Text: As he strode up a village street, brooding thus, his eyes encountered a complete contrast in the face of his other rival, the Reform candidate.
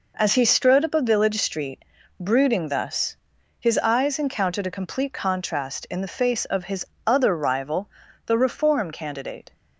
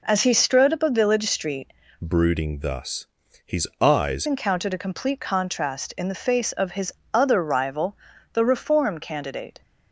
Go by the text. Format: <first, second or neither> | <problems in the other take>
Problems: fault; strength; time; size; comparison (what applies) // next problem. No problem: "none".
first | changes voice from "brooding" to "eyes"; from 2.0 to 4.2 s; 2.2 s long // pauses between "his" and "other"; slight; at 6.9 s; 0.18 s long; slight in the first